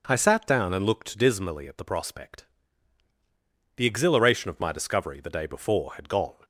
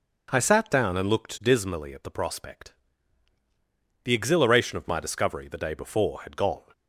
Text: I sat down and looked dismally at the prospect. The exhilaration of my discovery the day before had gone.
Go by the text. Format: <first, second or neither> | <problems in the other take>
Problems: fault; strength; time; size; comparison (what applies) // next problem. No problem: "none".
neither | none